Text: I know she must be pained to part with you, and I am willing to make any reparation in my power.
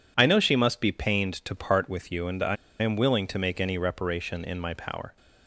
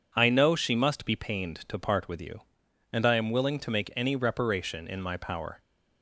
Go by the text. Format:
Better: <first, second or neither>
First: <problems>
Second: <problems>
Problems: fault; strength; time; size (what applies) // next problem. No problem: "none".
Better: second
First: pauses between "I" and "am"; slight; at 2.5 s; 0.26 s long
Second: none